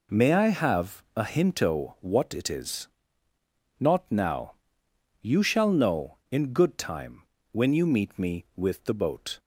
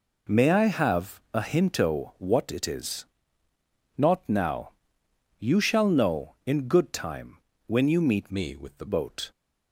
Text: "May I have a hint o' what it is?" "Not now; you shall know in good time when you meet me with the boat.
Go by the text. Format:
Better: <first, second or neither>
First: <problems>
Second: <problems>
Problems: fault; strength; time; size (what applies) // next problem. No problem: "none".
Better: first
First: pauses between "time" and "when"; slight; at 7.2 s; 0.28 s long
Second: pauses between "time" and "when"; slight; at 7.3 s; 0.28 s long // changes voice from "me" to "the"; from 8.3 to 8.8 s; 0.5 s long